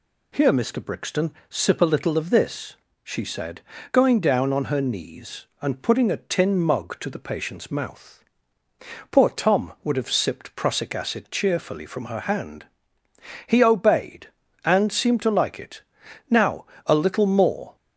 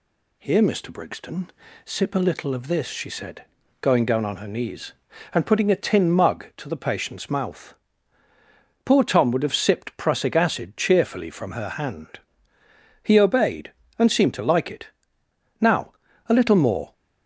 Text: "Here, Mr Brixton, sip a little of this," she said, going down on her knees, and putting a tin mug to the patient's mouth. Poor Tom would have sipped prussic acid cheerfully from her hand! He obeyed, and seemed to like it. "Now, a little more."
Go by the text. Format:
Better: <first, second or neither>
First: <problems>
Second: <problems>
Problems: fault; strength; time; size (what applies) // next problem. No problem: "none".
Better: neither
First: none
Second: none